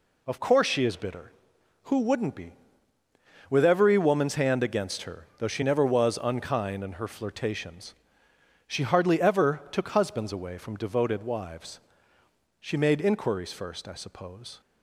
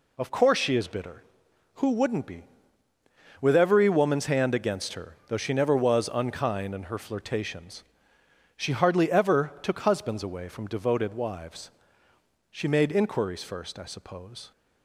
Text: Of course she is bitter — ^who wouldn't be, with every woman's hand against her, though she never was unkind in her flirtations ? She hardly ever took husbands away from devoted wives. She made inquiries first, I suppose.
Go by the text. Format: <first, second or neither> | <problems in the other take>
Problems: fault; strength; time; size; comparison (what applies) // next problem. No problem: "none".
neither | none